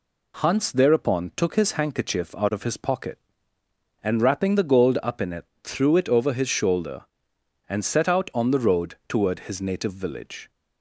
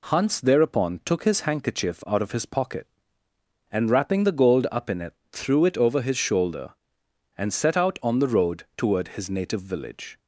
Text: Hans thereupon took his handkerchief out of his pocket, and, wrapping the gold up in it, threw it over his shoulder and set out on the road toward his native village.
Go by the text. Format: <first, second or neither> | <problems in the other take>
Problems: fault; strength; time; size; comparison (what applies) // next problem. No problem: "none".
neither | none